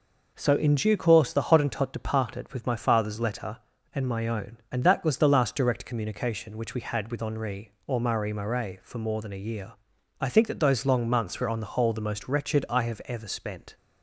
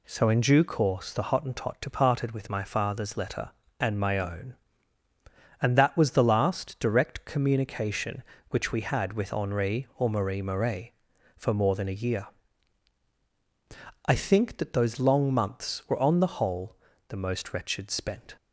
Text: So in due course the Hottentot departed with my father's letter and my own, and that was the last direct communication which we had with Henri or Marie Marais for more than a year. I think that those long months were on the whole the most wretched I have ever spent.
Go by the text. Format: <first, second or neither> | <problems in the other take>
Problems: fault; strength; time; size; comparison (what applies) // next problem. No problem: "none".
first | pauses between "whole" and "the"; slight; at 16.7 s; 0.32 s long // skips "I have ever"; at 17.8 s